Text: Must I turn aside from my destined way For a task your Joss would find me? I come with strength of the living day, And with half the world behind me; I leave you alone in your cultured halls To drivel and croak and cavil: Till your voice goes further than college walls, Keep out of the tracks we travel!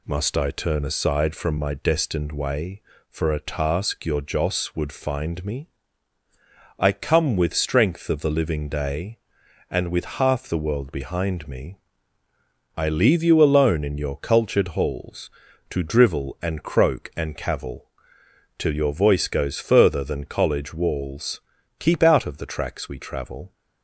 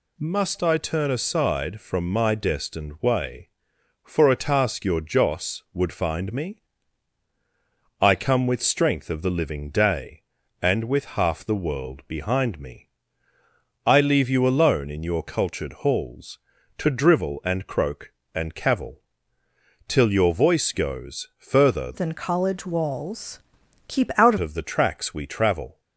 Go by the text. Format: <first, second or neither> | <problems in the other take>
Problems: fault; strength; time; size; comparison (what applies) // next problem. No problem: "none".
first | changes voice from "than" to "out"; from 21.9 to 24.3 s; 2.4 s long